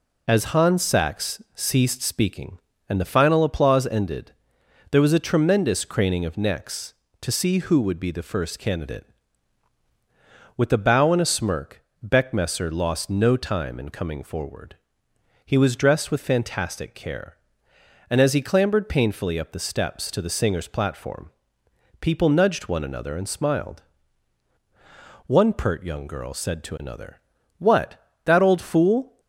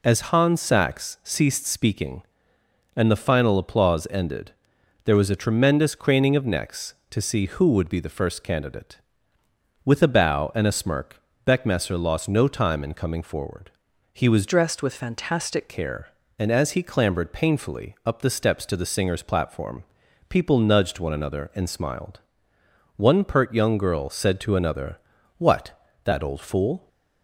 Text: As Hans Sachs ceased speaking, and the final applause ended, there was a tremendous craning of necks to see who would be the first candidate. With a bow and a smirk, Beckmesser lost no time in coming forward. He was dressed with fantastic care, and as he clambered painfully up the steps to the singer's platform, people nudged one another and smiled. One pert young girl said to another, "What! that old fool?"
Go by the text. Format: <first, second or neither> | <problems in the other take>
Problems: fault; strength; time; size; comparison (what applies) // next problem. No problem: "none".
first | changes voice from "dressed" to "fantastic"; from 14.4 to 15.6 s; 1.2 s long